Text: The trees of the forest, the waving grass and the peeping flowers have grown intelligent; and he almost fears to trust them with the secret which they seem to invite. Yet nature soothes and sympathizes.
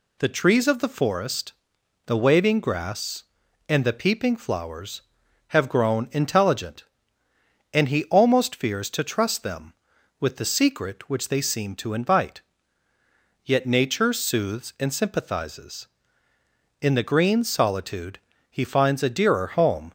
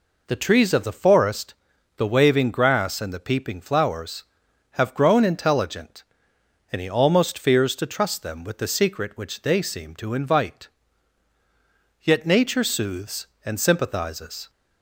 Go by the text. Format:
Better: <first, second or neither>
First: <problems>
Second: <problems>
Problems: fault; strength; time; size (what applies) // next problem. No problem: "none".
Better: second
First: goes on to say "In the green solitude he finds a dearer home"; strong; from 16.7 s on; 3.1 s long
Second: none